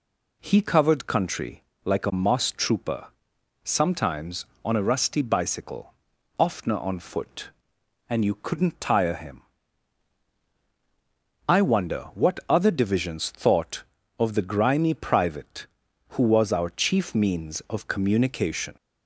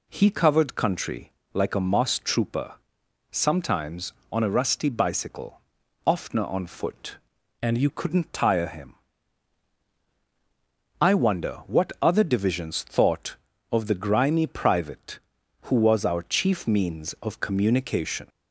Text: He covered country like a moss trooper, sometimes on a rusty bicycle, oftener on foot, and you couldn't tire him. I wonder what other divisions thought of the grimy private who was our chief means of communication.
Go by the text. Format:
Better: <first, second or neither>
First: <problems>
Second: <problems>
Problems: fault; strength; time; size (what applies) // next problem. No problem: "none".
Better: first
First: pauses between "country" and "like"; slight; at 1.6 s; 0.22 s long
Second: pauses between "country" and "like"; slight; at 1.3 s; 0.22 s long // changes voice from "and" to "you"; from 7.6 to 7.8 s; 0.2 s long